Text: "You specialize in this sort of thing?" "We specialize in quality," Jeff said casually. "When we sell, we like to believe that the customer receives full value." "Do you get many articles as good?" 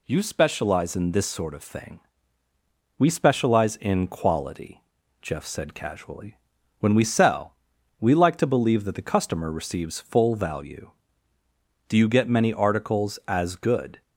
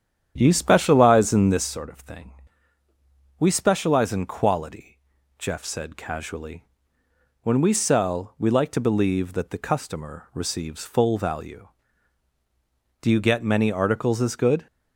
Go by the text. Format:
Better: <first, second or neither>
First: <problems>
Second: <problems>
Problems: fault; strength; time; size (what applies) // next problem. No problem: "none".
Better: first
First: none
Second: starts louder than the rest; strong; until 1.7 s; 9 dB